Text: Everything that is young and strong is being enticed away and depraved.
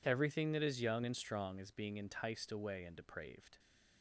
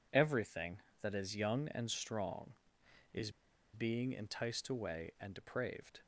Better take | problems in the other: first | pauses between "is" and "being"; at 3.2 s; 0.44 s long

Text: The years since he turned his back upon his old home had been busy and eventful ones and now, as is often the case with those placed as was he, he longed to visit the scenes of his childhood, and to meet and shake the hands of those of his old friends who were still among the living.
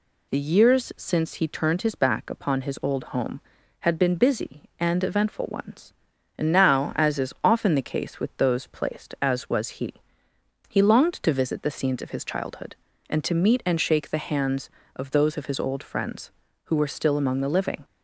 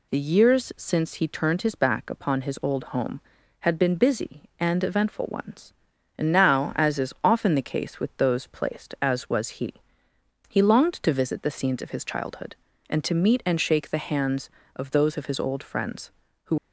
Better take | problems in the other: first | stops before "were still among the living"; at 16.5 s

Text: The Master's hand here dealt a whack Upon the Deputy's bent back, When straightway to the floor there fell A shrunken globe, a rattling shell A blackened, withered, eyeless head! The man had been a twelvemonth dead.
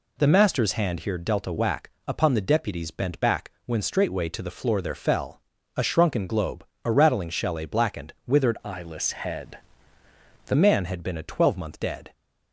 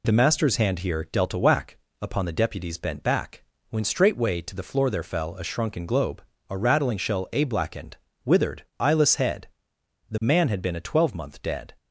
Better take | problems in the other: second | pauses between "whack" and "Upon"; slight; at 1.9 s; 0.16 s long; slight in the second // pauses between "fell" and "A"; slight; at 5.4 s; 0.34 s long // changes voice from "eyeless" to "The"; from 8.6 to 10.5 s; 1.9 s long

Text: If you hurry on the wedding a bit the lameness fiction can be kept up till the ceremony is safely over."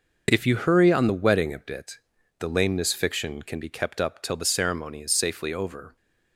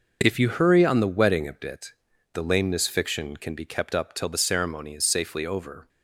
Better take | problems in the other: neither | pauses between "bit" and "the"; the same in both

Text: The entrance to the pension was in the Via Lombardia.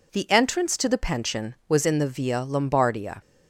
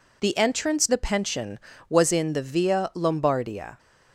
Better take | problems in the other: first | skips "to"; at 0.8 s

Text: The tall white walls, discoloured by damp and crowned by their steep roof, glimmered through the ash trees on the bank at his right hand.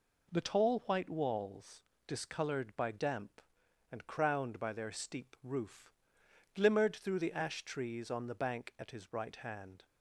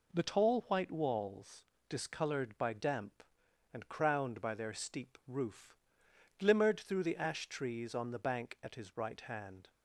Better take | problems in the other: neither | none

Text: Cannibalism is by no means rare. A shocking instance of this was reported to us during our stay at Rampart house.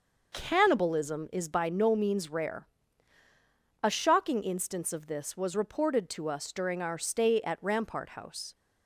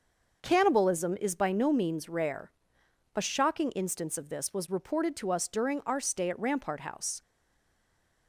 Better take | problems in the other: first | starts louder than the rest; until 1.4 s; 6.5 dB // stays silent after the last word; from 7.2 s on; 1.0 s long

